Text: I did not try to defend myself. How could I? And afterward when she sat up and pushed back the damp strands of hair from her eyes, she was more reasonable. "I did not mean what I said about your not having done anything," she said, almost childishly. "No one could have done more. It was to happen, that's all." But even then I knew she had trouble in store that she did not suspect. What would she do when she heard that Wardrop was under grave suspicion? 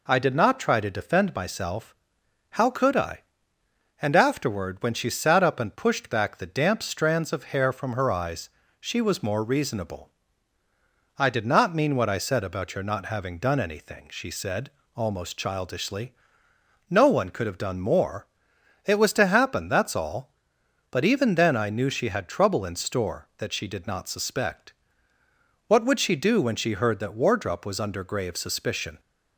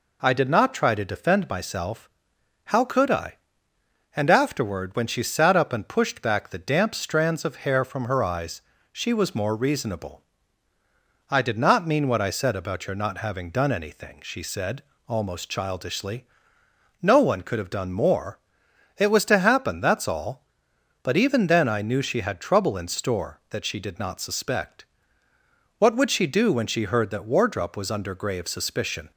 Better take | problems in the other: neither | none

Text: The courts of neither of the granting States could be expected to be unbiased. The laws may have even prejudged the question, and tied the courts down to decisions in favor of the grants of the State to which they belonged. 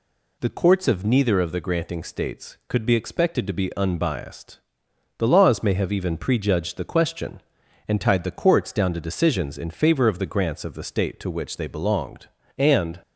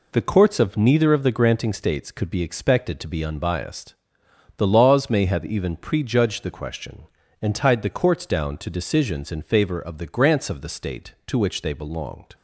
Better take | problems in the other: second | goes on to say "And"; slight; from 12.5 s on; 0.42 s long

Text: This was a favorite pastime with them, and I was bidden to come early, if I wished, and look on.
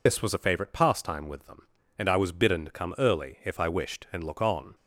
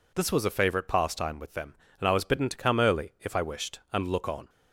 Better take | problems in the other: second | loses the start of "This"; at 0.0 s; 85 ms

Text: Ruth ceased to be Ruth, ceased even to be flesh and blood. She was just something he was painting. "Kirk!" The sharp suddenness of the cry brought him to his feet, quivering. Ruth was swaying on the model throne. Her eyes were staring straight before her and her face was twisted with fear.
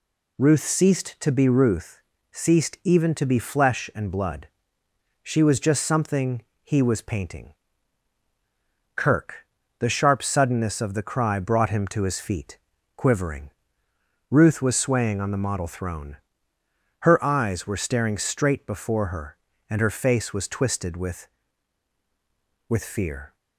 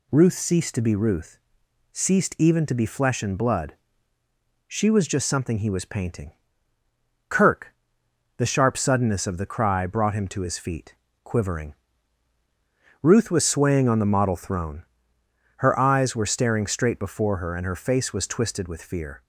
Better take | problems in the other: second | pauses between "something" and "he"; slight; at 6.4 s; 0.22 s long // says "with" twice; at 22.6 s

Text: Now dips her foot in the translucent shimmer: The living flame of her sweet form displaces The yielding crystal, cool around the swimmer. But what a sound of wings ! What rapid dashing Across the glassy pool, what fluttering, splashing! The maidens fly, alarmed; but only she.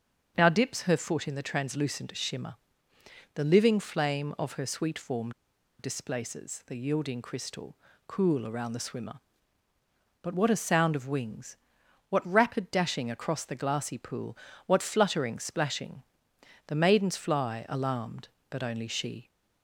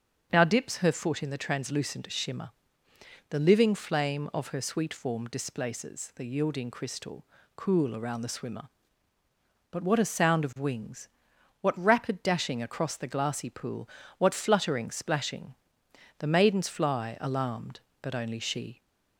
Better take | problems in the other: second | starts louder than the rest; until 1.3 s; 6.5 dB; also in the second // pauses between "form" and "displaces"; noticeable; at 5.3 s; 0.48 s long

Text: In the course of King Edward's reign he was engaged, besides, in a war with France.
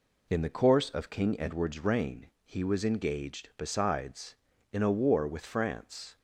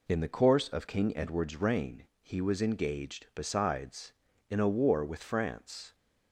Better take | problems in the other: neither | pauses between "reign" and "he"; slight; the same in both

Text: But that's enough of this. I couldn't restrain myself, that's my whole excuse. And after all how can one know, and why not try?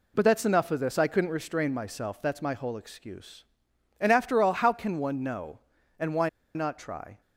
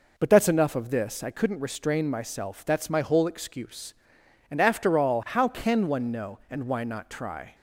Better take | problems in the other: second | pauses between "why" and "not"; slight; at 6.2 s; 0.26 s long

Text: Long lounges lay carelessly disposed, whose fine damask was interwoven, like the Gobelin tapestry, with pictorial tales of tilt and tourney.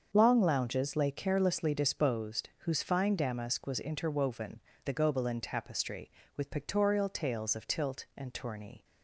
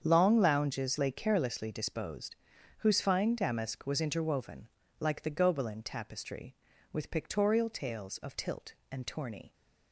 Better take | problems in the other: second | starts louder than the rest; until 1.1 s; 6.5 dB; strong in the second // skips "like"; at 4.7 s

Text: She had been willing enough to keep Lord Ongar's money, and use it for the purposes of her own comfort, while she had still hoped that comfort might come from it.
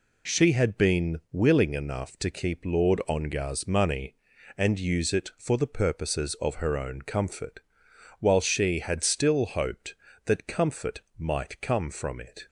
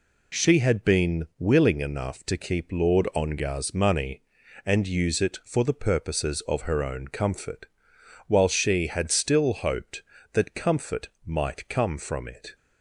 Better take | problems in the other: neither | pauses between "comfort" and "might"; slight; the same in both

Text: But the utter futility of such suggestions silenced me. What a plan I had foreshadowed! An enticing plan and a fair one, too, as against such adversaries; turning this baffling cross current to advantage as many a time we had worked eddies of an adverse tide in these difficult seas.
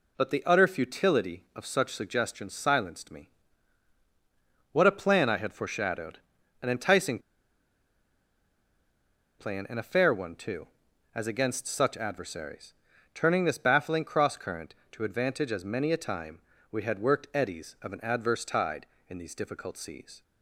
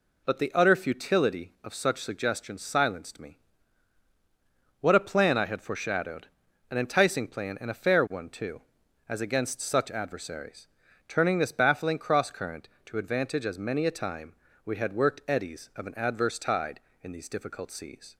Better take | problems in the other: second | pauses between "enticing" and "plan"; strong; at 7.1 s; 2.2 s long // pauses between "time" and "we"; slight; at 16.3 s; 0.30 s long; slight in the second

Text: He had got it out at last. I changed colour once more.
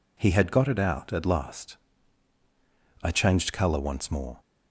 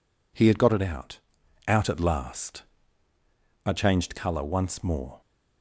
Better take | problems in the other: first | says "out" twice; at 1.6 s

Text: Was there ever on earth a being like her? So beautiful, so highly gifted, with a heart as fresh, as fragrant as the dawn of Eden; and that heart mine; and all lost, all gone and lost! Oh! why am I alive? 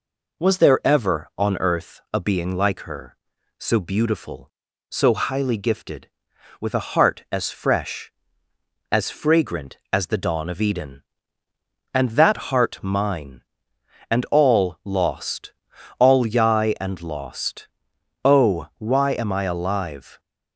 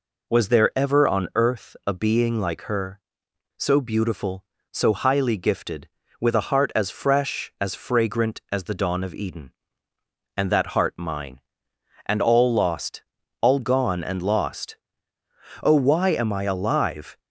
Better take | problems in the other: second | says "yai" for "gone"; at 16.2 s

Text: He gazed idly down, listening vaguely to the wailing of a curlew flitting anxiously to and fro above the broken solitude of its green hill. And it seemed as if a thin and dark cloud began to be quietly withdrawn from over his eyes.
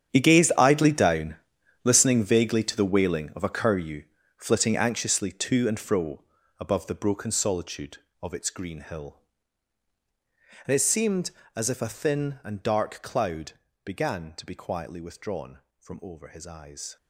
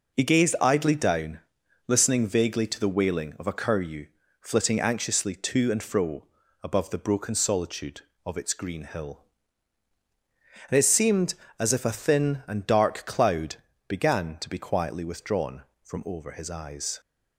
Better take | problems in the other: second | gets quieter; strong; throughout; 15.5 dB // pauses between "curlew" and "flitting"; slight; at 4.0 s; 0.36 s long; slight in the second // pauses between "fro" and "above"; slight; at 6.2 s; 0.34 s long; slight in the second // pauses between "cloud" and "began"; slight; at 13.5 s; 0.32 s long; slight in the second

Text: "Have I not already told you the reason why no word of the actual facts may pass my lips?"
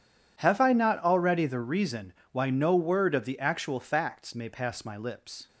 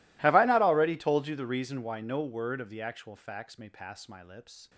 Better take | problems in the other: second | skips "told you"; at 1.4 s // pauses between "reason" and "why"; slight; at 2.1 s; 0.22 s long

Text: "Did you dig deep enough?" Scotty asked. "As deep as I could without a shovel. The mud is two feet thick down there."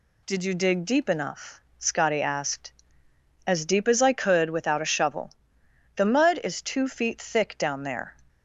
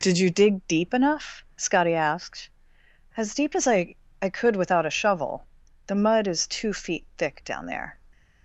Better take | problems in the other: first | says "I" twice; at 4.1 s

